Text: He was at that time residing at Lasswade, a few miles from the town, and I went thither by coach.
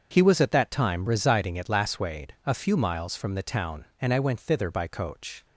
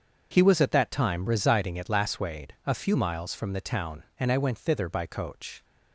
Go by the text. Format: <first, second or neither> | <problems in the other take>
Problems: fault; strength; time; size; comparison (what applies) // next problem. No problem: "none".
neither | starts louder than the rest; the same in both